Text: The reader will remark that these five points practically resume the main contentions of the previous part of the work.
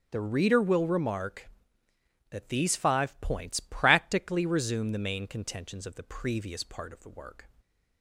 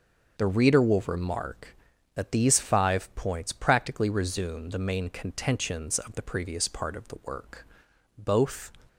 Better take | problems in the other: first | starts louder than the rest; until 1.4 s; 6.5 dB; strong in the first // goes on to say "Both"; from 8.1 s on; 0.56 s long

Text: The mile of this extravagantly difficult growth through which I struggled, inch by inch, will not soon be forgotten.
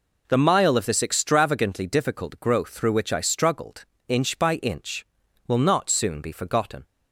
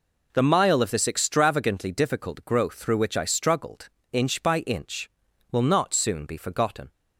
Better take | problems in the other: neither | none

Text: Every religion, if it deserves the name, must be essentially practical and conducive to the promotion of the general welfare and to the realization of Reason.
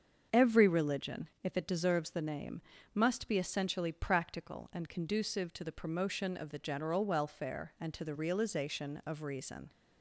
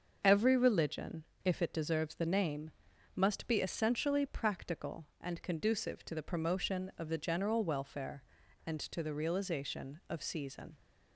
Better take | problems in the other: first | starts louder than the rest; until 1.2 s; 6.5 dB; also in the first // says "Season" for "Reason"; at 10.2 s

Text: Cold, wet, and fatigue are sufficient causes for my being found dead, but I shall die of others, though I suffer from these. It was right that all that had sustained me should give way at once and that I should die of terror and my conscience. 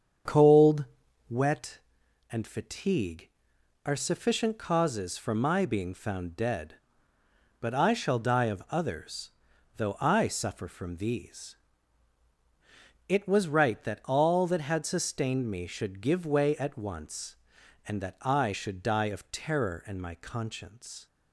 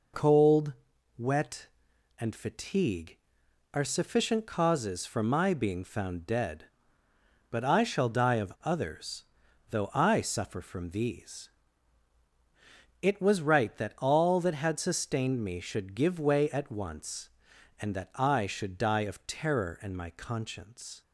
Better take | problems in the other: second | starts louder than the rest; strong; until 1.6 s; 7.5 dB

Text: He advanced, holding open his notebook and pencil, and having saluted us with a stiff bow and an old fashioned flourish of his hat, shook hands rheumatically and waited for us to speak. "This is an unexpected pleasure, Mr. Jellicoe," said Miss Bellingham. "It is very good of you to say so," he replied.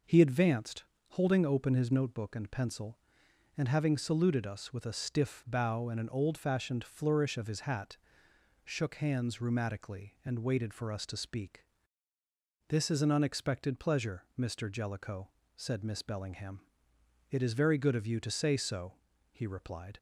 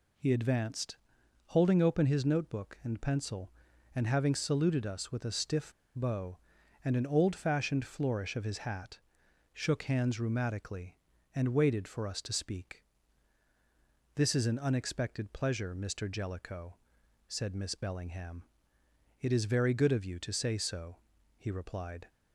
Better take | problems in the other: first | pauses between "stiff" and "bow"; slight; at 5.7 s; 0.24 s long

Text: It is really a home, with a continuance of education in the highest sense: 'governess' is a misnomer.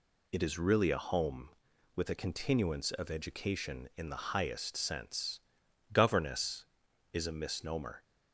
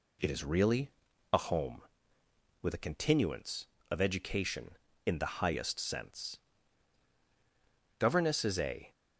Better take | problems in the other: first | pauses between "really" and "a"; at 0.8 s; 0.42 s long // stops before "misnomer"; at 8.9 s

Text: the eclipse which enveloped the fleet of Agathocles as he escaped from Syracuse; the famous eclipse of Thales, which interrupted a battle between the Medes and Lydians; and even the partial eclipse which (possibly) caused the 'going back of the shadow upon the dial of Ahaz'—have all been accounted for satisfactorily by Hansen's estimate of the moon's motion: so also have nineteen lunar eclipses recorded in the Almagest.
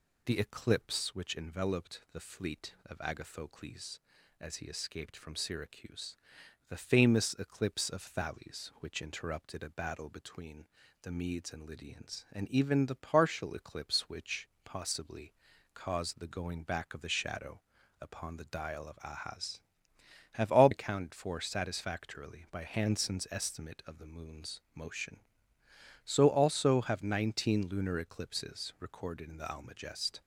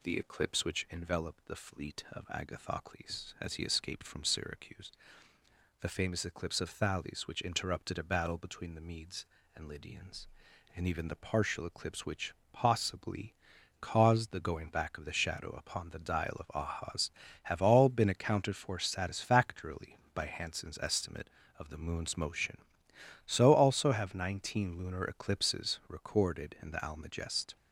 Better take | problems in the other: second | pauses between "between" and "the"; slight; at 10.6 s; 0.36 s long // pauses between "shadow" and "upon"; at 17.6 s; 0.40 s long // skips "been"; at 20.6 s

